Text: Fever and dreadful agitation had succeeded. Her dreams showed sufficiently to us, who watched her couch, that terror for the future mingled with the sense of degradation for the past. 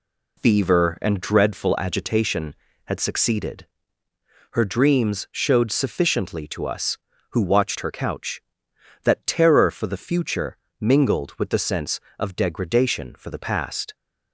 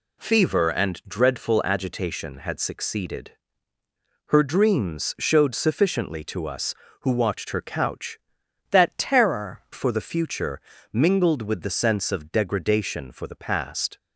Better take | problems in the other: first | changes voice from "that" to "terror"; from 8.7 to 9.6 s; 0.9 s long // pauses between "future" and "mingled"; slight; at 10.6 s; 0.30 s long; slight in the first

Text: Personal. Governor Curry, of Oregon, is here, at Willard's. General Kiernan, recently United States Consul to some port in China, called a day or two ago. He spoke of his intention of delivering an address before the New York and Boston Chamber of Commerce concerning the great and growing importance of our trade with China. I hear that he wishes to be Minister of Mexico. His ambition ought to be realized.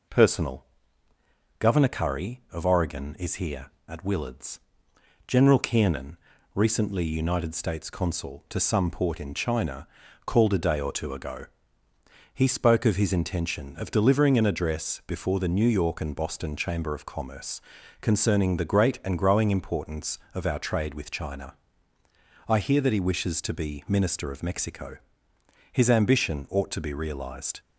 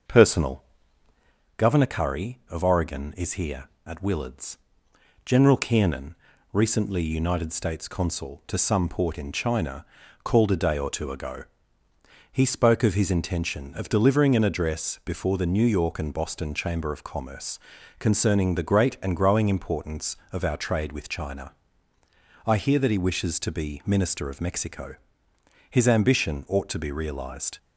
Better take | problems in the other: first | starts louder than the rest; until 1.5 s; 6 dB // pauses between "Commerce" and "concerning"; at 17.5 s; 0.40 s long; also in the first

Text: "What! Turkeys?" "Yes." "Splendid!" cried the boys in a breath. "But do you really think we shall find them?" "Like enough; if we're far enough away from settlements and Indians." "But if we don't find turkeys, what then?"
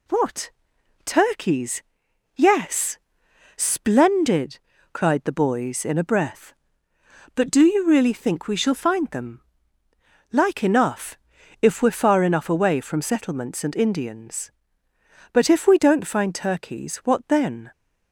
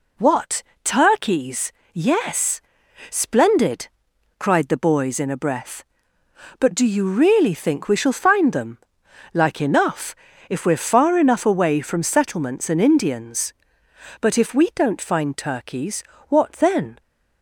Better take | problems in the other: neither | none

